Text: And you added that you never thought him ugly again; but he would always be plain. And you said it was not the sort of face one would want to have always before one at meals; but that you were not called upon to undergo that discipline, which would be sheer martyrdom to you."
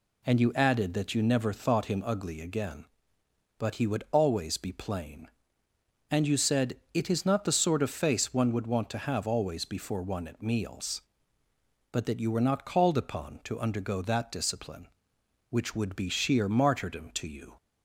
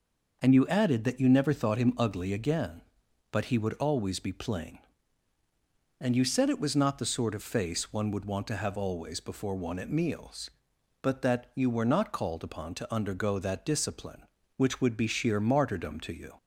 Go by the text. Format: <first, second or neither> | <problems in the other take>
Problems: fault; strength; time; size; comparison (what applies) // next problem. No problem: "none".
second | pauses between "said" and "it"; slight; at 6.7 s; 0.16 s long // says "is" for "was"; at 7.1 s